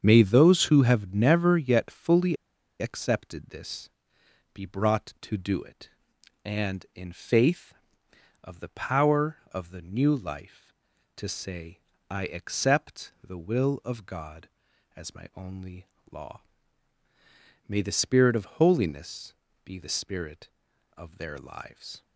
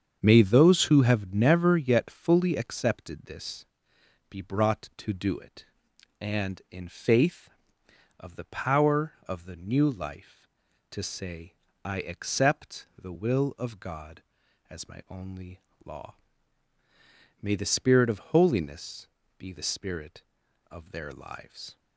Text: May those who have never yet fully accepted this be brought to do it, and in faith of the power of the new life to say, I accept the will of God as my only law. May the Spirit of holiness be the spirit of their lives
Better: second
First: starts louder than the rest; strong; until 1.0 s; 7.5 dB // pauses between "fully" and "accepted"; at 2.3 s; 0.45 s long // pauses between "this" and "be"; noticeable; at 3.8 s; 0.64 s long // pauses between "only" and "law"; slight; at 15.8 s; 0.24 s long // pauses between "holiness" and "be"; slight; at 19.3 s; 0.32 s long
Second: starts louder than the rest; strong; until 1.2 s; 7.5 dB // pauses between "this" and "be"; noticeable; at 3.6 s; 0.64 s long // pauses between "only" and "law"; slight; at 15.6 s; 0.24 s long // pauses between "holiness" and "be"; slight; at 19.0 s; 0.32 s long

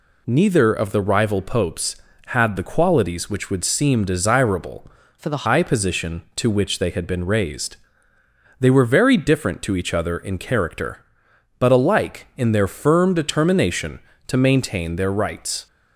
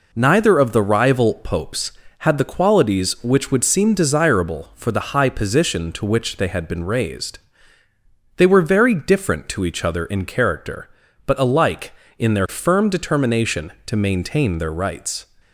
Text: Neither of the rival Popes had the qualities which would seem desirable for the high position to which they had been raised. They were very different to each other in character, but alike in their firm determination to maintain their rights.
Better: second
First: changes voice from "for" to "the"; from 5.1 to 5.4 s; 0.3 s long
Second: none

